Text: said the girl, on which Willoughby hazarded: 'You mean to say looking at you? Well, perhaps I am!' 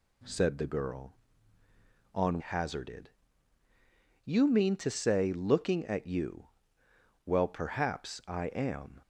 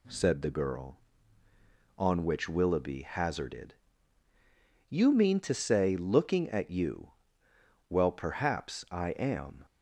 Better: second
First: skips "which Willoughby"; at 2.3 s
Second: none

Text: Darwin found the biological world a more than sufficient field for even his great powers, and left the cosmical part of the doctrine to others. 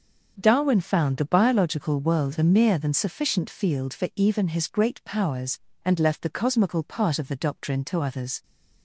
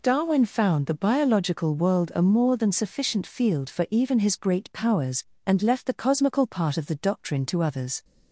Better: second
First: starts louder than the rest; until 1.3 s; 6.5 dB // says "mere" for "more"; at 2.4 s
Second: none

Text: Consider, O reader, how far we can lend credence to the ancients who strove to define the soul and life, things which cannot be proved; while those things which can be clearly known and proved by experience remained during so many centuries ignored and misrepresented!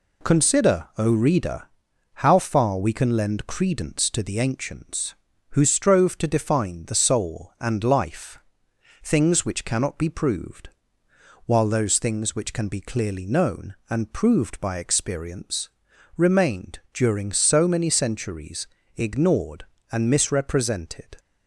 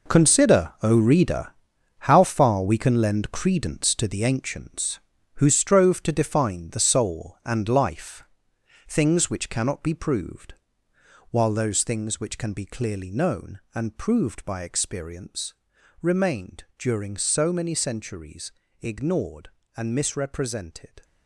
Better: first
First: pauses between "experience" and "remained"; noticeable; at 15.6 s; 0.46 s long // pauses between "remained" and "during"; slight; at 16.7 s; 0.16 s long // pauses between "centuries" and "ignored"; slight; at 18.6 s; 0.28 s long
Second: gets quieter; strong; throughout; 12 dB // pauses between "experience" and "remained"; noticeable; at 15.5 s; 0.46 s long // pauses between "remained" and "during"; slight; at 16.6 s; 0.16 s long // pauses between "centuries" and "ignored"; slight; at 18.5 s; 0.28 s long

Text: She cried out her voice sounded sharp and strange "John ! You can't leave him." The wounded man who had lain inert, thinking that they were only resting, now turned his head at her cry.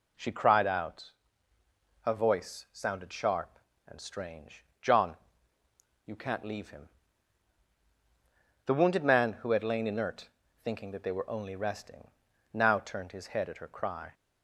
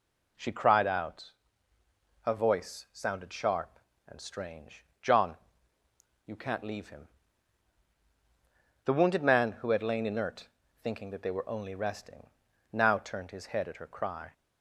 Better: neither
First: pauses between "out" and "her"; noticeable; at 1.1 s; 0.92 s long // pauses between "strange" and "John"; slight; at 4.6 s; 0.16 s long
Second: pauses between "out" and "her"; noticeable; at 1.3 s; 0.92 s long // pauses between "strange" and "John"; slight; at 4.8 s; 0.16 s long

